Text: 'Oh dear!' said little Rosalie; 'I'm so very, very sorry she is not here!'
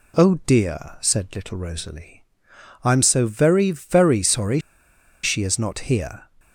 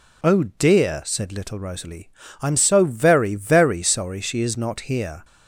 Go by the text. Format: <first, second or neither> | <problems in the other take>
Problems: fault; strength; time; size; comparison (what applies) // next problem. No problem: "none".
second | pauses between "sorry" and "she"; noticeable; at 4.6 s; 0.62 s long